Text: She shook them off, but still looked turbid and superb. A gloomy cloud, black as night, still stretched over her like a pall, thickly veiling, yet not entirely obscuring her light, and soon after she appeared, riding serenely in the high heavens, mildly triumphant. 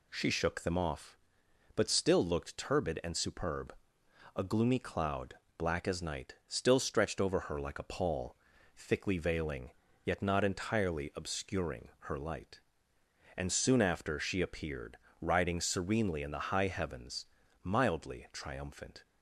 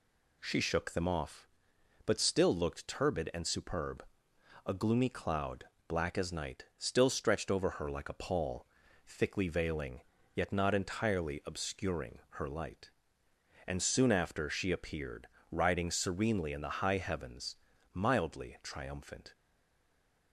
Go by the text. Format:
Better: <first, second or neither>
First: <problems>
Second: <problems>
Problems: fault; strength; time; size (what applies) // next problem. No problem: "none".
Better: first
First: none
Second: stays silent after the last word; from 19.3 s on; 1.0 s long